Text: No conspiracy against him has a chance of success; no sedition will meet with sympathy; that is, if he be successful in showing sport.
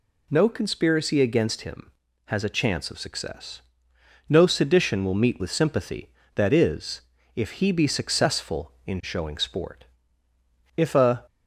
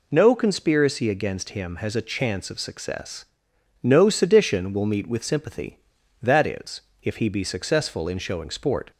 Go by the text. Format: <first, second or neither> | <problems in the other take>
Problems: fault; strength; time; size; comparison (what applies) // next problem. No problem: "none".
second | goes on to say "If a"; slight; from 10.7 s on; 0.48 s long